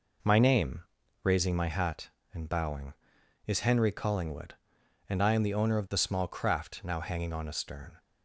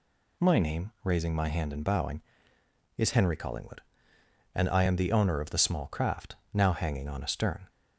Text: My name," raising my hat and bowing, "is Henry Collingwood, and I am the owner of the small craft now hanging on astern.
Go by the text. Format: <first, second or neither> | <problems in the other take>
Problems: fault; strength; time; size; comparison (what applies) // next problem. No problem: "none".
first | says "hand" for "hat"; at 1.4 s // pauses between "craft" and "now"; slight; at 6.3 s; 0.18 s long